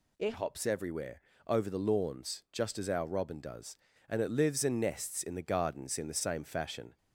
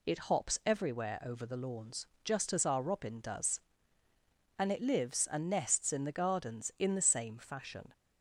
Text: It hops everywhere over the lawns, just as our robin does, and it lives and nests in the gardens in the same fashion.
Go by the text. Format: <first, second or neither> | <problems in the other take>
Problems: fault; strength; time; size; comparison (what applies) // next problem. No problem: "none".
second | changes voice at "hops"; from 0.3 s on; 6.6 s long // pauses between "everywhere" and "over"; slight; at 1.2 s; 0.24 s long